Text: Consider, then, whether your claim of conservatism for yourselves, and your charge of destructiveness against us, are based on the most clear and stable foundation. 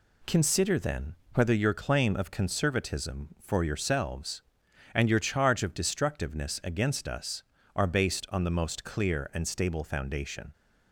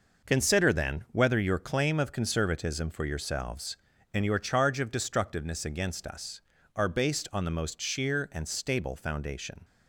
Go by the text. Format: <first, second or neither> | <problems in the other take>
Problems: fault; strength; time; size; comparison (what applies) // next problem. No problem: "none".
first | says "sheer" for "clear"; at 7.8 s